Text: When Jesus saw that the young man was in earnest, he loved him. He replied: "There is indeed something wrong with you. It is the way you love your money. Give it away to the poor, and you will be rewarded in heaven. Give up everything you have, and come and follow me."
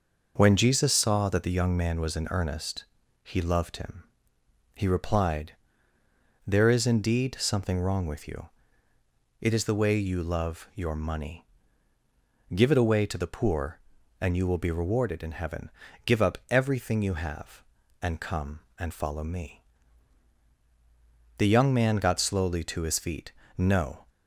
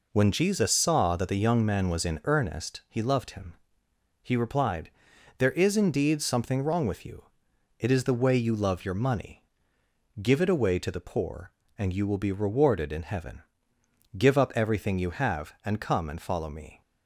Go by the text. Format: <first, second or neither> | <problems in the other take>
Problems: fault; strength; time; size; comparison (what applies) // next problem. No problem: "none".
second | starts louder than the rest; noticeable; until 1.3 s; 6 dB // goes on to say "The young man got slowly to his feet No"; strong; from 21.3 s on; 2.6 s long